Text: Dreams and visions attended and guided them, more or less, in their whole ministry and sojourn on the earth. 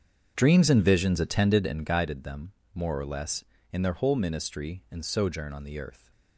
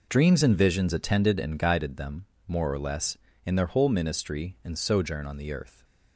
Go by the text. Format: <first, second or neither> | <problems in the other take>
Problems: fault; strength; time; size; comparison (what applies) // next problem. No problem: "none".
second | starts louder than the rest; strong; until 1.9 s; 7.5 dB